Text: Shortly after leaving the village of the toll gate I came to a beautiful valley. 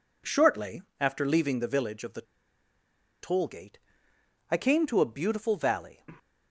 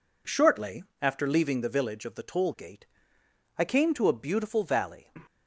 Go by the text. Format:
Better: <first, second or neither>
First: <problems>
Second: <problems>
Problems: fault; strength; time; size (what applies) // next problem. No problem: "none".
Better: second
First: pauses between "Shortly" and "after"; slight; at 0.8 s; 0.18 s long // pauses between "the" and "toll"; at 2.2 s; 0.99 s long // pauses between "gate" and "I"; noticeable; at 3.7 s; 0.72 s long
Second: pauses between "Shortly" and "after"; slight; at 0.8 s; 0.18 s long // pauses between "gate" and "I"; noticeable; at 2.8 s; 0.72 s long